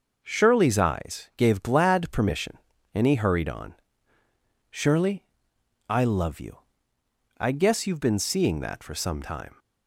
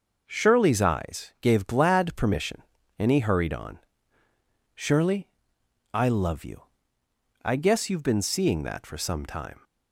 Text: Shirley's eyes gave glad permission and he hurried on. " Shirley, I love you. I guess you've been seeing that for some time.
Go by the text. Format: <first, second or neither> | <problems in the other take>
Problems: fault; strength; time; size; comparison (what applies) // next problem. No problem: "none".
neither | starts louder than the rest; noticeable; the same in both